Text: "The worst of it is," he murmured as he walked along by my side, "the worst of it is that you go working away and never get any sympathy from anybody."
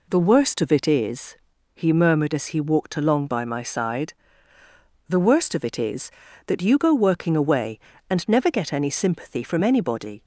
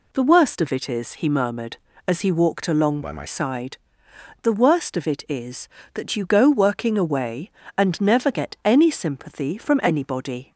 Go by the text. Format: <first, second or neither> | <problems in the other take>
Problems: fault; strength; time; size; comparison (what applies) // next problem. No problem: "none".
first | changes voice from "by" to "my"; from 3.0 to 3.2 s; 0.2 s long